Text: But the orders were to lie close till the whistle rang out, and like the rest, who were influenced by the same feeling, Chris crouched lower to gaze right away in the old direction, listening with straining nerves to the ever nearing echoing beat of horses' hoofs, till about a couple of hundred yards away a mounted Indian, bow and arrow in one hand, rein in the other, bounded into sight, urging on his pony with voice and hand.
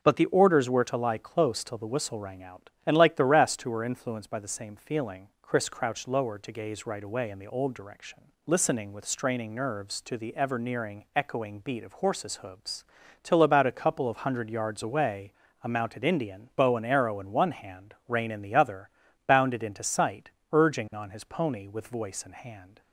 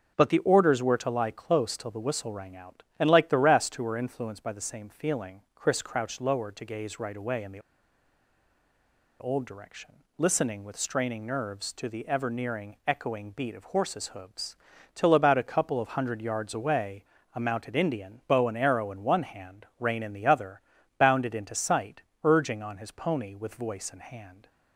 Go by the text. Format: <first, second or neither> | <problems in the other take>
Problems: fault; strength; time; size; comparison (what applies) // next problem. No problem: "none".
first | starts louder than the rest; until 1.1 s; 6.5 dB; also in the first // pauses between "the" and "old"; strong; at 7.5 s; 1.6 s long // pauses between "away" and "a"; slight; at 17.0 s; 0.30 s long; slight in the first